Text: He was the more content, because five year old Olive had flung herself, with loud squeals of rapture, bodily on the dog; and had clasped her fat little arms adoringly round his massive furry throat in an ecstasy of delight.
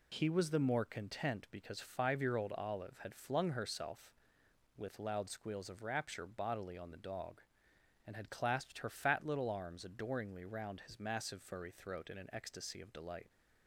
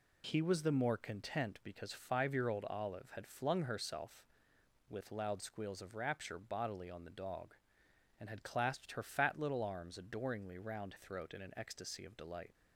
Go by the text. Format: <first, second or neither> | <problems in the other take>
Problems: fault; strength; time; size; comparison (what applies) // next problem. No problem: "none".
first | skips "his massive furry"; at 10.9 s